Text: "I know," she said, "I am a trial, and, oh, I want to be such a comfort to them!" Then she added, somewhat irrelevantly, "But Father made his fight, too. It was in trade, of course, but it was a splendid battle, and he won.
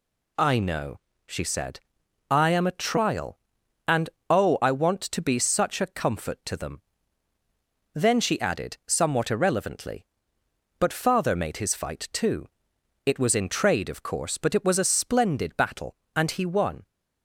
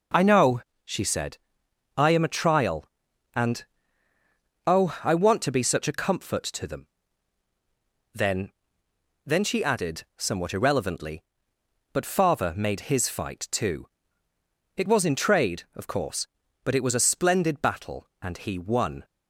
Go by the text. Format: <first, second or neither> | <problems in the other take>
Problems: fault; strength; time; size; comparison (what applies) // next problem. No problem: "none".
first | says "Then" twice; at 9.2 s